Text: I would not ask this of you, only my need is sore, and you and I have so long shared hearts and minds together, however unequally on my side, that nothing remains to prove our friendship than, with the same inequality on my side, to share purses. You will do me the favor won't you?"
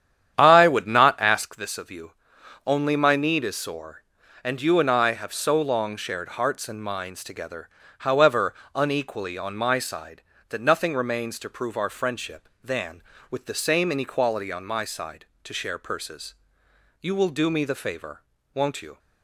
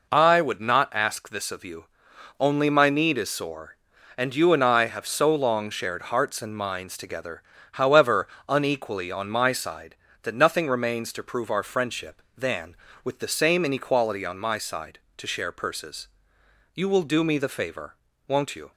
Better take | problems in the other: second | starts louder than the rest; strong; until 1.5 s; 9.5 dB // pauses between "however" and "unequally"; slight; at 8.5 s; 0.22 s long; slight in the second // pauses between "favor" and "won't"; slight; at 18.2 s; 0.34 s long; slight in the second

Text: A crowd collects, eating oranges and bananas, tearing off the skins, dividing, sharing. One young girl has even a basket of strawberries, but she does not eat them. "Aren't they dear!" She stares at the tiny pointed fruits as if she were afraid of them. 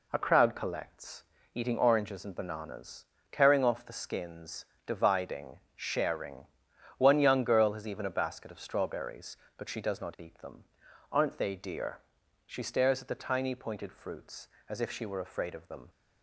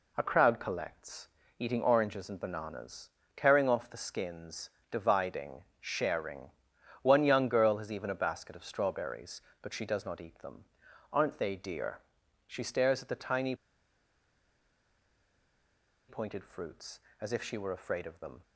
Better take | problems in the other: first | pauses between "tiny" and "pointed"; strong; at 13.5 s; 2.5 s long

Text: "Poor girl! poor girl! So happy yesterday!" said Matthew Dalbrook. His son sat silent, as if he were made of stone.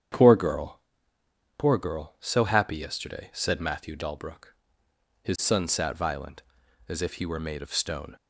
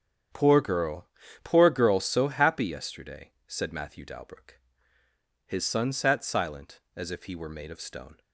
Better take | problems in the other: second | starts louder than the rest; strong; until 1.9 s; 9 dB; strong in the second // says "violent" for "silent"; at 5.9 s

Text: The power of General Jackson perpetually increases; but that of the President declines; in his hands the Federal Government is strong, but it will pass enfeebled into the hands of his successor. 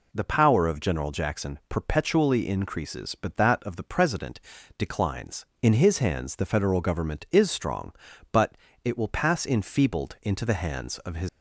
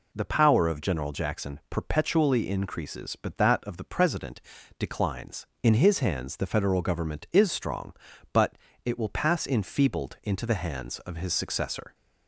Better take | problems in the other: second | pauses between "President" and "declines"; at 4.3 s; 0.40 s long; also in the second // pauses between "but" and "it"; slight; at 8.5 s; 0.26 s long; slight in the second // stops before "successor"; at 11.2 s

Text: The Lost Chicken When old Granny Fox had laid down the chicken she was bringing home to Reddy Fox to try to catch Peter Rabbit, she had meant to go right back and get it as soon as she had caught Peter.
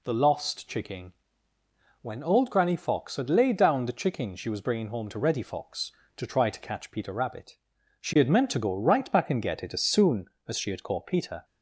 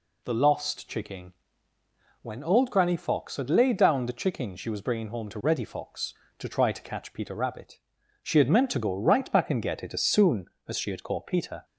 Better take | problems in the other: neither | pauses between "Chicken" and "When"; noticeable; the same in both

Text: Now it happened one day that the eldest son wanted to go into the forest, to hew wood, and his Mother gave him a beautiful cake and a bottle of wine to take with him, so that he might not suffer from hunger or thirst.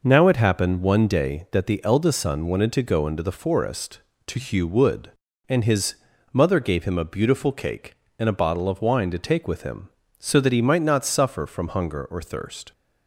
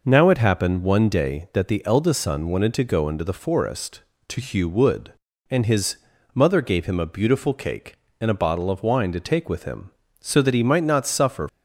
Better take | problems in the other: first | pauses between "his" and "Mother"; at 5.9 s; 0.38 s long; also in the first // stops before "from hunger or thirst"; at 11.4 s

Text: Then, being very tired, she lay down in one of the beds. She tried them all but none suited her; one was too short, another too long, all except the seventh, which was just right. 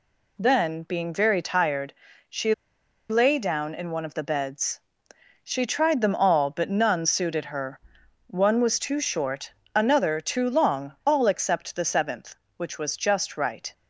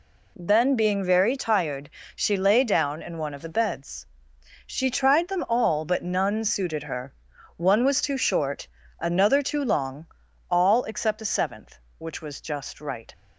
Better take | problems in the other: second | pauses between "she" and "lay"; noticeable; at 2.5 s; 0.56 s long

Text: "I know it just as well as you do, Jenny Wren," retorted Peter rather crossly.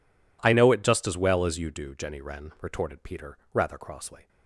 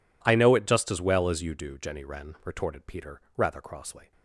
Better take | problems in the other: neither | pauses between "Peter" and "rather"; slight; the same in both

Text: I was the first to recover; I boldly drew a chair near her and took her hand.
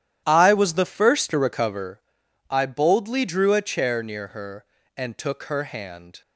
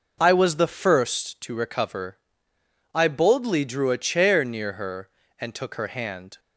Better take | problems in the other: second | starts louder than the rest; strong; until 2.1 s; 11 dB

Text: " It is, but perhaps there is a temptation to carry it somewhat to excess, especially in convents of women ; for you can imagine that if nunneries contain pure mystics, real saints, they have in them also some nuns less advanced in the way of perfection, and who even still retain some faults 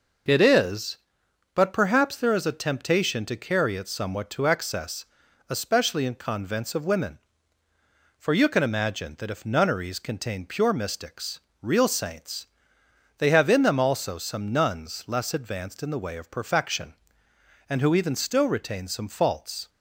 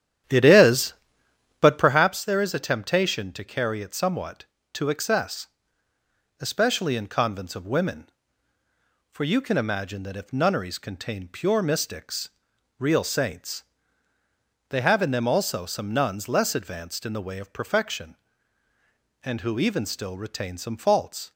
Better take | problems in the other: first | starts louder than the rest; strong; until 2.1 s; 10.5 dB

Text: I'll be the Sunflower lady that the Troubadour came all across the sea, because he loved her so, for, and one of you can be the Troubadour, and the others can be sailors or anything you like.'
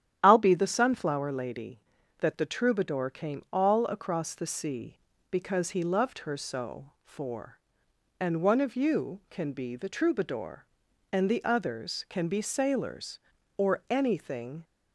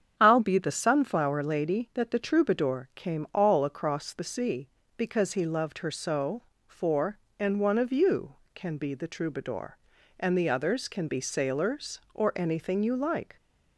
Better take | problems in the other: second | starts louder than the rest; strong; until 1.2 s; 10.5 dB; strong in the second // stops before "you like"; at 14.6 s

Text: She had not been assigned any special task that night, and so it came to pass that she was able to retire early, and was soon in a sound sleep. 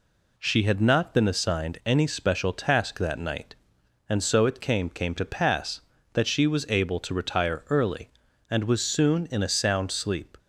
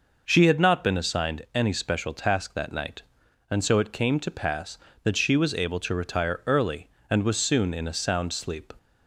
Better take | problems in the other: second | says "came" twice; at 4.9 s

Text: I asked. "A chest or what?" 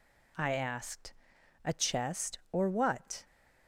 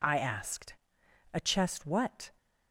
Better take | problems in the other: first | skips "or"; at 1.8 s

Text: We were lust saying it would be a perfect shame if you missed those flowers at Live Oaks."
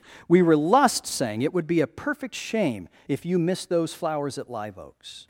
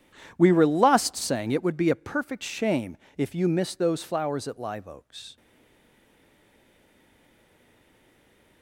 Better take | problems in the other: first | pauses between "shame" and "if"; slight; at 2.9 s; 0.22 s long; slight in the first // stays silent after the last word; strong; from 5.3 s on; 3.3 s long

